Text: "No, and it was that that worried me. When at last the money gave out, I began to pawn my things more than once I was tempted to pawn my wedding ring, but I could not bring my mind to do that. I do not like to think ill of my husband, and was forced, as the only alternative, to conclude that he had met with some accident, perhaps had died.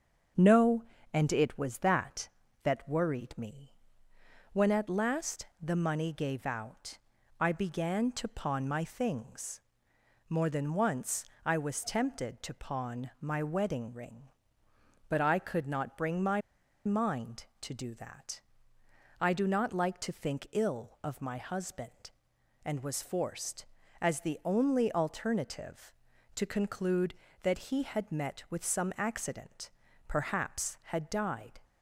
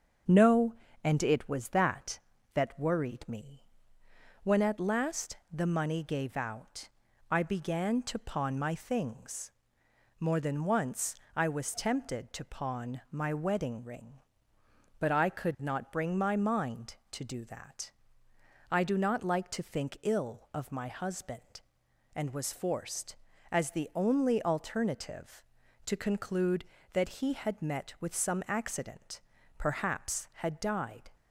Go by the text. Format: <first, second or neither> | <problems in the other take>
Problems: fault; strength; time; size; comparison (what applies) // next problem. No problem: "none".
second | starts louder than the rest; until 1.6 s; 7 dB; also in the second // pauses between "last" and "the"; slight; at 5.4 s; 0.16 s long; slight in the second // pauses between "things" and "more"; noticeable; at 9.6 s; 0.66 s long; noticeable in the second // pauses between "once" and "I"; slight; at 11.2 s; 0.22 s long; slight in the second // pauses between "my" and "mind"; at 16.4 s; 0.44 s long